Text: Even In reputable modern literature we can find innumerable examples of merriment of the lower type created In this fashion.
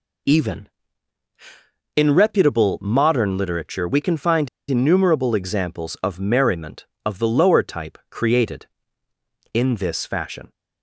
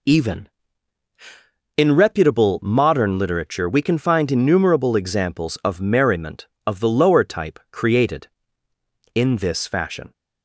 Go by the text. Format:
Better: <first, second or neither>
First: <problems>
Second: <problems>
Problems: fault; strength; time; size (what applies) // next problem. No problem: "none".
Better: second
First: pauses between "find" and "innumerable"; slight; at 4.4 s; 0.22 s long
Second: none